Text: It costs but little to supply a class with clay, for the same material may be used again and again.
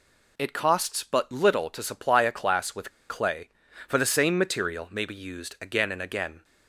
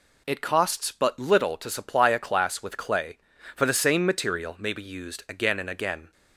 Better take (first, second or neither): second